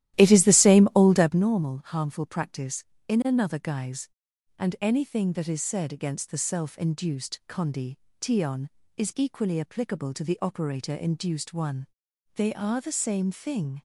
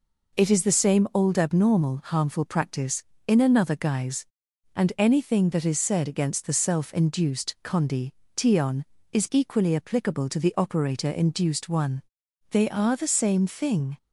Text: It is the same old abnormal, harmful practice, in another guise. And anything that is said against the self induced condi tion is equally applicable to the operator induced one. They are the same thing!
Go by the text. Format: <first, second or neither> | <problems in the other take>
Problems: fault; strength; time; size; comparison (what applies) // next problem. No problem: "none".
second | starts louder than the rest; strong; until 1.5 s; 13.5 dB // pauses between "condi" and "tion"; slight; at 7.9 s; 0.24 s long; slight in the second